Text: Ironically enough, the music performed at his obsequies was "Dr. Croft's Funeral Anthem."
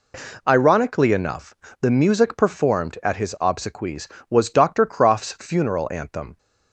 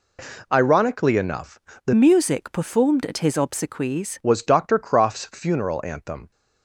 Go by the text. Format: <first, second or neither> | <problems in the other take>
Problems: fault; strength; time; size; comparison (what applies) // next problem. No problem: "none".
first | changes voice from "music" to "obsequies"; from 1.9 to 4.1 s; 2.2 s long